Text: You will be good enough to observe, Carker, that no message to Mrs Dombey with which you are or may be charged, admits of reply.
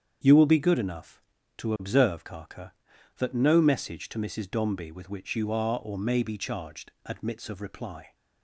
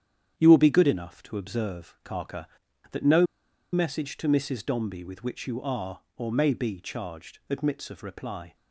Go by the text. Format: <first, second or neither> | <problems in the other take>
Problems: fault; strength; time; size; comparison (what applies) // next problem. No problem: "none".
first | starts louder than the rest; strong; until 1.3 s; 9.5 dB; strong in the first // pauses between "no" and "message"; noticeable; at 3.2 s; 0.48 s long